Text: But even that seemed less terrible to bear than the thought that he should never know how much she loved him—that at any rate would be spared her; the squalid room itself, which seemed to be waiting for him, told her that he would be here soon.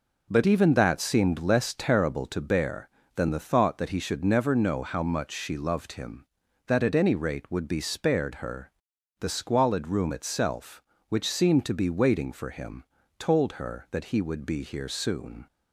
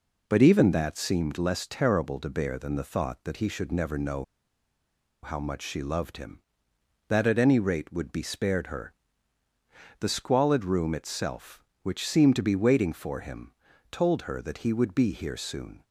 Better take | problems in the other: first | pauses between "know" and "how"; at 4.2 s; 0.98 s long

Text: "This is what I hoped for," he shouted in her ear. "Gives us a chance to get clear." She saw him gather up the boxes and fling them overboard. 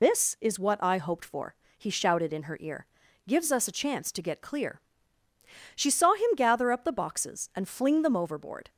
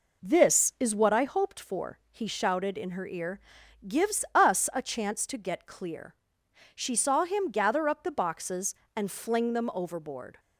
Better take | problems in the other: second | loses the start of "This"; at 0.0 s; 65 ms

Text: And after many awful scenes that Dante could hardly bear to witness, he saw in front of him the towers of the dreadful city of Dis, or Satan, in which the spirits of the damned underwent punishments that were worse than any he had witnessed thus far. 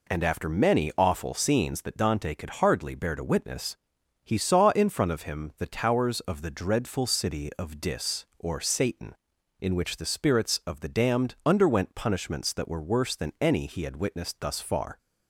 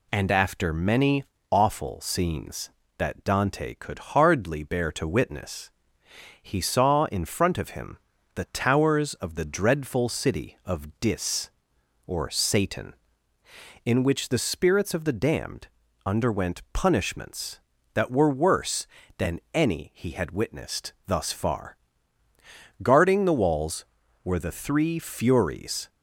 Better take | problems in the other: first | pauses between "many" and "awful"; slight; at 1.2 s; 0.26 s long // pauses between "him" and "the"; slight; at 7.9 s; 0.36 s long // pauses between "damned" and "underwent"; at 15.6 s; 0.40 s long // goes on to say "Guarding the walls were the three Furies"; strong; from 22.8 s on; 3.0 s long

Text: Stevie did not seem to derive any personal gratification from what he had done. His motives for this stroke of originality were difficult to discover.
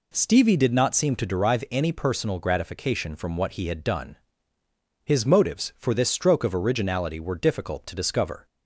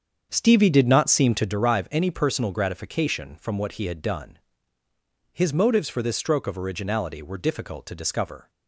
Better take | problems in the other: first | starts louder than the rest; strong; until 1.5 s; 7.5 dB

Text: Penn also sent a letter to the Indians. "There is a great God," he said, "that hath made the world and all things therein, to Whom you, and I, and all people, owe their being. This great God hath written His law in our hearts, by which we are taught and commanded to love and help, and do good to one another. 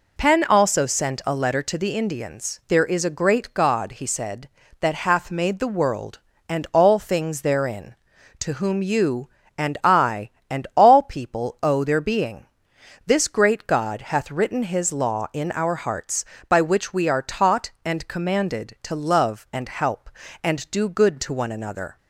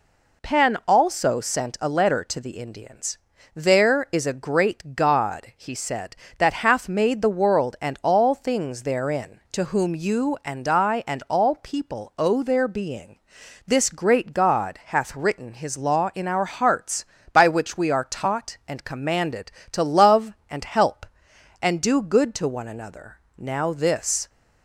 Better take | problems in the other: first | goes on to say "Now this"; noticeable; from 23.3 s on; 0.92 s long

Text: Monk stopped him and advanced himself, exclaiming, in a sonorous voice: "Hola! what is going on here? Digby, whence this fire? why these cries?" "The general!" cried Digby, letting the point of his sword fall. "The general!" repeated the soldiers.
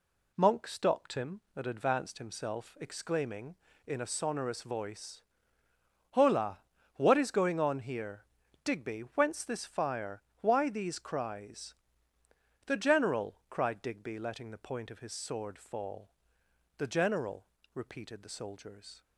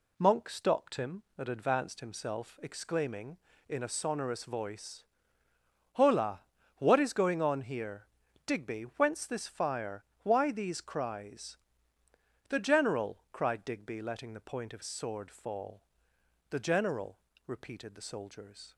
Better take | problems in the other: first | skips "his"; at 14.8 s

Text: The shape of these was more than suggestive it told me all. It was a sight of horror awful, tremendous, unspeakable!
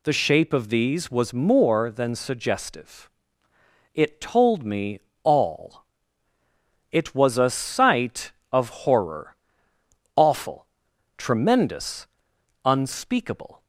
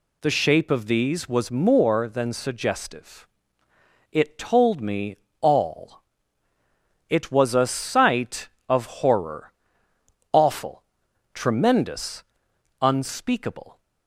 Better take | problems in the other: neither | pauses between "suggestive" and "it"; noticeable; the same in both // pauses between "me" and "all"; slight; the same in both // pauses between "horror" and "awful"; noticeable; the same in both

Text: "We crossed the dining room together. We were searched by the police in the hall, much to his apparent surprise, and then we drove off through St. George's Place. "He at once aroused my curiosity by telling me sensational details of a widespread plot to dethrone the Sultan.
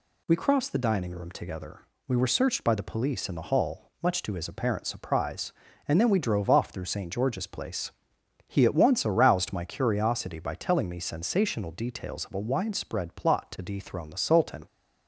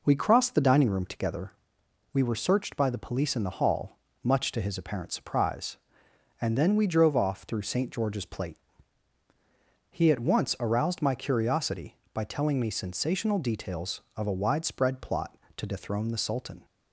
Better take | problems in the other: first | says "Plate" for "Place"; at 8.2 s

